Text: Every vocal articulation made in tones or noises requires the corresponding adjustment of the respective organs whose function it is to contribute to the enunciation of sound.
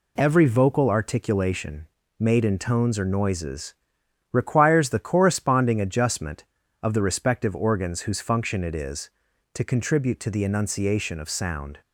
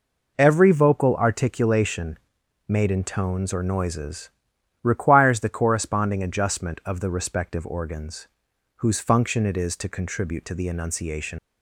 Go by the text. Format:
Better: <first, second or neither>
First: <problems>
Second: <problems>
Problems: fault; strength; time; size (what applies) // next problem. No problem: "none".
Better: first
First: pauses between "articulation" and "made"; slight; at 1.8 s; 0.30 s long // pauses between "noises" and "requires"; noticeable; at 3.7 s; 0.58 s long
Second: pauses between "articulation" and "made"; noticeable; at 2.1 s; 0.48 s long // pauses between "noises" and "requires"; noticeable; at 4.3 s; 0.52 s long // pauses between "organs" and "whose"; noticeable; at 8.2 s; 0.50 s long // stops before "of sound"; at 11.3 s